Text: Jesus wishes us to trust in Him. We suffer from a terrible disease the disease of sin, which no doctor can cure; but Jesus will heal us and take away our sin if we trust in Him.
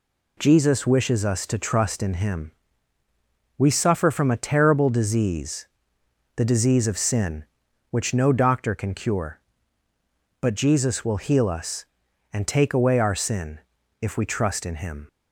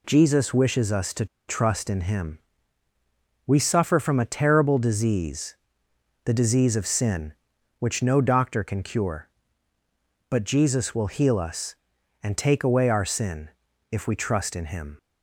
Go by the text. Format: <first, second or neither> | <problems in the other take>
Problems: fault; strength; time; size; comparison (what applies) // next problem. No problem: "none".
first | pauses between "to" and "trust"; slight; at 1.2 s; 0.22 s long // pauses between "disease" and "the"; noticeable; at 5.5 s; 0.68 s long; noticeable in the first // pauses between "sin" and "if"; at 13.4 s; 0.42 s long; also in the first